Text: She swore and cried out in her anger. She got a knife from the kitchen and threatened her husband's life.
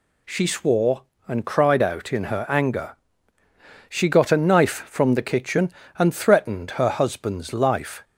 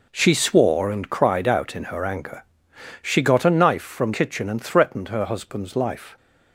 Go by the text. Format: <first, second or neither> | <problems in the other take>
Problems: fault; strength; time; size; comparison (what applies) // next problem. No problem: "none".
first | skips "the"; at 4.1 s